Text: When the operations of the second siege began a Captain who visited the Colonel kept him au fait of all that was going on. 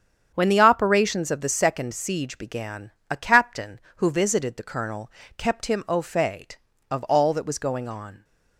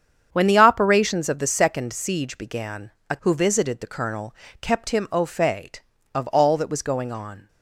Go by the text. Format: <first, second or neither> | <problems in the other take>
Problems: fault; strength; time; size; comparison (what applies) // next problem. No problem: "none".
first | starts louder than the rest; strong; until 1.3 s; 8 dB; strong in the first // pauses between "began" and "a"; slight; at 2.9 s; 0.18 s long; slight in the first // skips "Captain"; at 3.1 s // pauses between "Colonel" and "kept"; slight; at 4.3 s; 0.24 s long; slight in the first